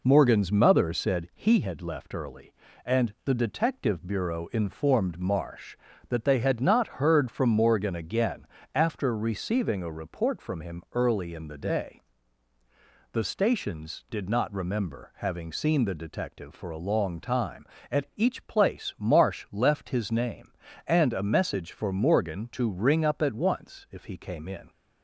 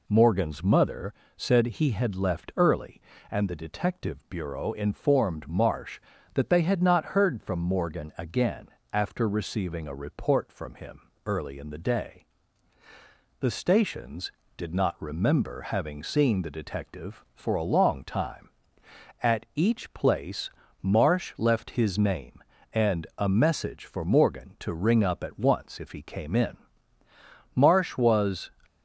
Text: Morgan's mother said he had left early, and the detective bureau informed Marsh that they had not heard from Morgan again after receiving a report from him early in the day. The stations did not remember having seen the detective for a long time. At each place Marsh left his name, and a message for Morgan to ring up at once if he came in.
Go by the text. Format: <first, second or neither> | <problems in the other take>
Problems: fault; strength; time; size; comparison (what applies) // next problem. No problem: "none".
first | pauses between "mother" and "said"; slight; at 1.1 s; 0.22 s long // pauses between "again" and "after"; slight; at 8.6 s; 0.24 s long; slight in the first // pauses between "him" and "early"; slight; at 11.0 s; 0.24 s long // pauses between "place" and "Marsh"; slight; at 20.4 s; 0.32 s long // goes on to say "Marsh was"; noticeable; from 27.5 s on; 0.96 s long